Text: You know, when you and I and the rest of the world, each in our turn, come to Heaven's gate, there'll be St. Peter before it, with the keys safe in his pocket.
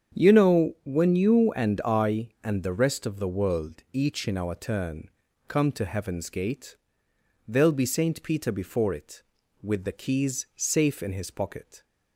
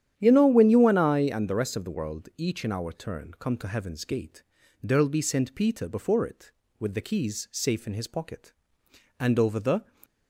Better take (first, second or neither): first